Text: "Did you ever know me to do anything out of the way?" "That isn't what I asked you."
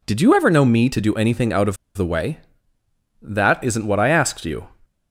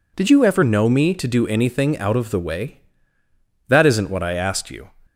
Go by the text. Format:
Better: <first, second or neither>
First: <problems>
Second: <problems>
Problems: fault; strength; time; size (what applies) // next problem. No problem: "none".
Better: second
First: pauses between "of" and "the"; slight; at 1.7 s; 0.20 s long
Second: none